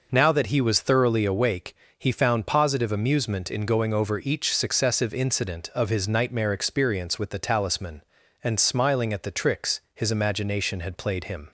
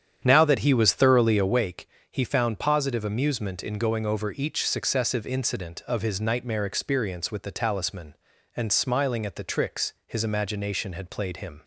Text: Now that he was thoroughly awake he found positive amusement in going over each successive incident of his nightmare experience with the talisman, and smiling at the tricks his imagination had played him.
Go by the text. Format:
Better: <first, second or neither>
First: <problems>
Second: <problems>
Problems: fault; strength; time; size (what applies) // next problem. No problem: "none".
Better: first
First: pauses between "awake" and "he"; slight; at 1.7 s; 0.22 s long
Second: starts louder than the rest; strong; until 1.7 s; 9 dB // pauses between "awake" and "he"; slight; at 1.8 s; 0.22 s long